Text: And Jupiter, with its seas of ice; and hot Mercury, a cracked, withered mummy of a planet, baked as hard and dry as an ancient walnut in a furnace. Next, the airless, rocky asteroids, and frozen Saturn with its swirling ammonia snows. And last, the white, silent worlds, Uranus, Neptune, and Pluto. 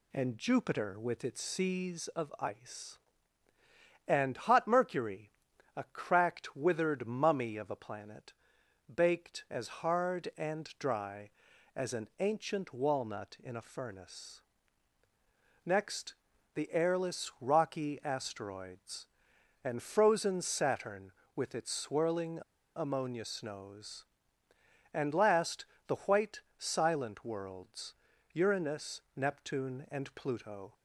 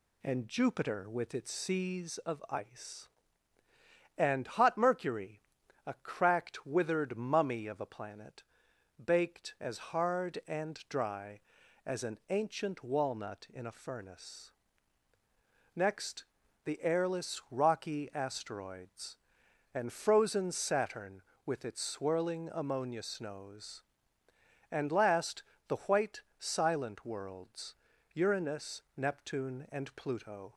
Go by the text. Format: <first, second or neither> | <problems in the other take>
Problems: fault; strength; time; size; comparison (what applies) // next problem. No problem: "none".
second | pauses between "swirling" and "ammonia"; slight; at 22.4 s; 0.35 s long